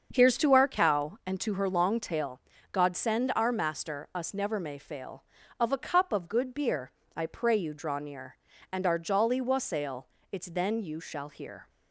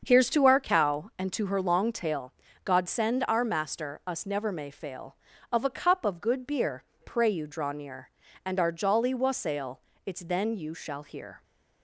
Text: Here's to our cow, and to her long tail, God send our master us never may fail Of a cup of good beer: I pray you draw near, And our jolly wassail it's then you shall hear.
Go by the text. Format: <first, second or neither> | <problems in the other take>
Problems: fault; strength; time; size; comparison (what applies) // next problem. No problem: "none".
first | starts louder than the rest; until 1.0 s; 6.5 dB; also in the first // skips "I"; at 6.9 s // pauses between "wassail" and "it's"; slight; at 9.8 s; 0.26 s long; slight in the first